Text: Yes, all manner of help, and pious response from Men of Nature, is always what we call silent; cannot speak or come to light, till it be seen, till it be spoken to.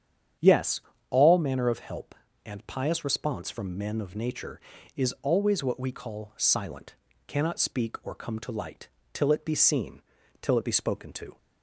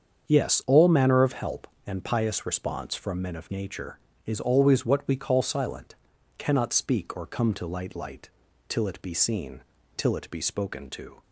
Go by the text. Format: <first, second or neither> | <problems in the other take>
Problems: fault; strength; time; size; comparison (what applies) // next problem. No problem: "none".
first | starts louder than the rest; strong; until 1.3 s; 7.5 dB; strong in the first // says "light" twice; at 7.9 s